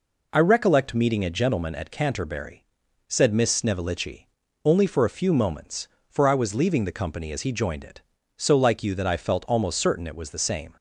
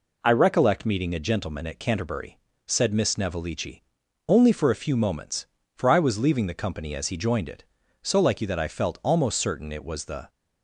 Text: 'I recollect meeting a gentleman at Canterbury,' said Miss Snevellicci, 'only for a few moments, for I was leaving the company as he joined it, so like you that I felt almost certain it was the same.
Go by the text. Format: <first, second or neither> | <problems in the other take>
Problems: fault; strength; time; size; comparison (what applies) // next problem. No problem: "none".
first | stops before "same"; at 10.2 s